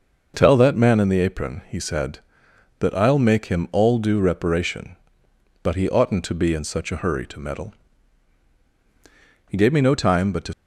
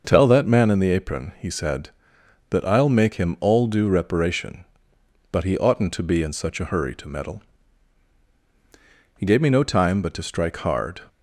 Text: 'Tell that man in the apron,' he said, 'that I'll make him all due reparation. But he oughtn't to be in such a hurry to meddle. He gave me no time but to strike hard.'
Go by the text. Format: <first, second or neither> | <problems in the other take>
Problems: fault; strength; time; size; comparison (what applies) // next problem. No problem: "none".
second | stops before "strike hard"; at 10.5 s